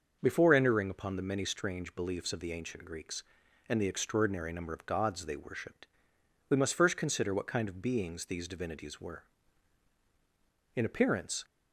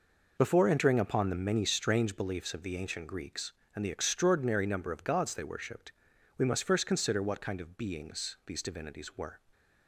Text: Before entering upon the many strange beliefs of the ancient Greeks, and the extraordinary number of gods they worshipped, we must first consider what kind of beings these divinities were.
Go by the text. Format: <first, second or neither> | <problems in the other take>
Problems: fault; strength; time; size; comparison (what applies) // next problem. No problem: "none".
second | starts louder than the rest; until 1.2 s; 6 dB // goes on to say "In appearance"; noticeable; from 10.7 s on; 0.70 s long